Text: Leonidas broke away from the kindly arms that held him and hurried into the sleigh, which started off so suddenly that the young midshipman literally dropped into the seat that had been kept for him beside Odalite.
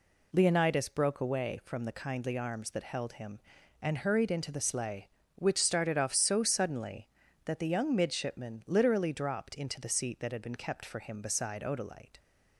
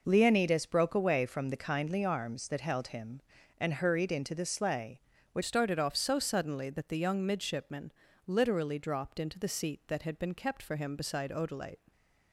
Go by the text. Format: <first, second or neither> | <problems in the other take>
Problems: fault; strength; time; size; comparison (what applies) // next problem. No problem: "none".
first | changes voice at "started"; from 5.4 s on; 6.5 s long // pauses between "midshipman" and "literally"; slight; at 7.9 s; 0.34 s long